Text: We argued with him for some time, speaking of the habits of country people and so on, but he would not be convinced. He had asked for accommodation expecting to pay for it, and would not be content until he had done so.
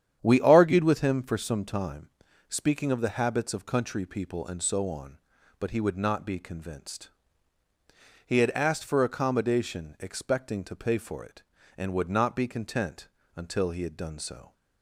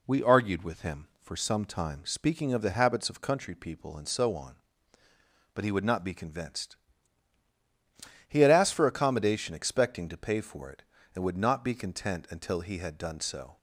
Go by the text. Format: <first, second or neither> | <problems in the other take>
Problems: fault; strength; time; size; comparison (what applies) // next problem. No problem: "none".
second | starts louder than the rest; strong; until 1.5 s; 9.5 dB // pauses between "content" and "until"; slight; at 13.0 s; 0.28 s long